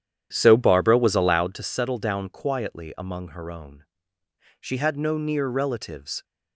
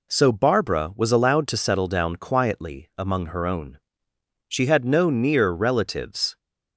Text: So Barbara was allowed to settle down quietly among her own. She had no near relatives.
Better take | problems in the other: second | starts louder than the rest; strong; until 1.6 s; 10 dB

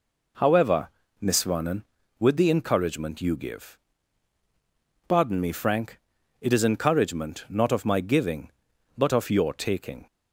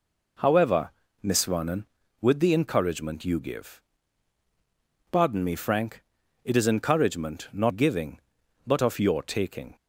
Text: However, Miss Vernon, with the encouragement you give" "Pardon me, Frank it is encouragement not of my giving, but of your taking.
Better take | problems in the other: first | pauses between "give" and "Pardon"; strong; at 3.8 s; 1.2 s long; strong in the first // pauses between "Frank" and "it"; at 6.0 s; 0.40 s long; also in the first // skips "of my"; at 7.7 s

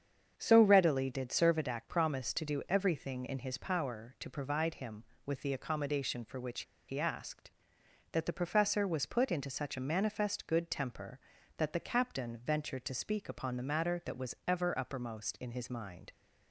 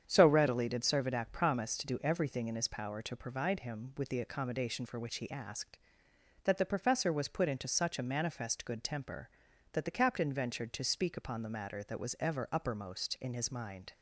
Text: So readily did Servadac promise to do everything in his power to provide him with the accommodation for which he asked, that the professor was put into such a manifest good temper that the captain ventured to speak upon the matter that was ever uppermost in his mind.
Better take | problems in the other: second | starts louder than the rest; strong; until 1.3 s; 7.5 dB; strong in the second // pauses between "which" and "he"; slight; at 6.6 s; 0.26 s long

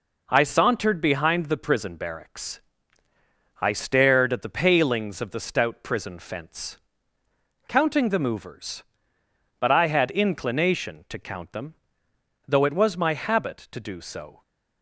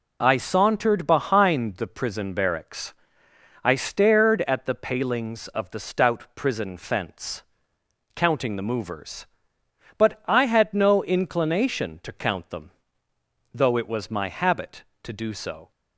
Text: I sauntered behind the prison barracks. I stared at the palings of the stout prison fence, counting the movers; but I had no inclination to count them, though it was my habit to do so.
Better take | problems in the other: second | skips "no"; at 10.0 s

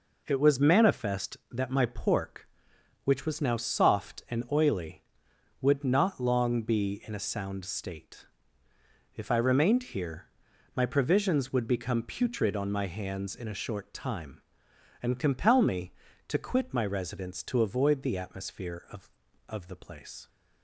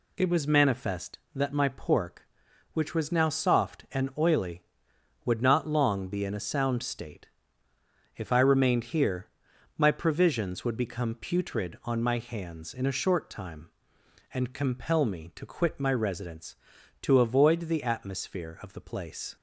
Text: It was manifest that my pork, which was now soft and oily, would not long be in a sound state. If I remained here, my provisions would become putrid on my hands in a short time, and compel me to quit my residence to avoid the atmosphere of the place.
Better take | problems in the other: second | says "of" twice; at 19.4 s

